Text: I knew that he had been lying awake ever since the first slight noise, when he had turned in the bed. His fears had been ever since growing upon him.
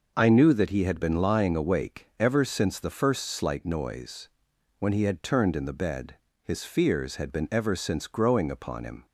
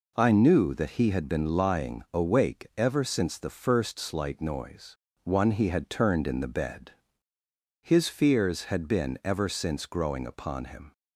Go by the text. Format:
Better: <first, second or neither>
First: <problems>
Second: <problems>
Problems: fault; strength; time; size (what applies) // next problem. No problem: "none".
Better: first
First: none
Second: says "one" for "when"; at 5.2 s